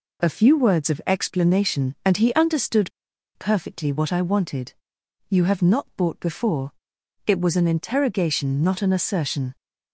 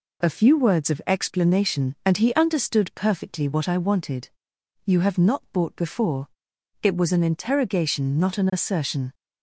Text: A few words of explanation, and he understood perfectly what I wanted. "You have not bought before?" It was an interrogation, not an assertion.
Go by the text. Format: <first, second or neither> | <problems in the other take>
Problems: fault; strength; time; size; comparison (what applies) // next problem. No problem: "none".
second | pauses between "understood" and "perfectly"; noticeable; at 2.9 s; 0.46 s long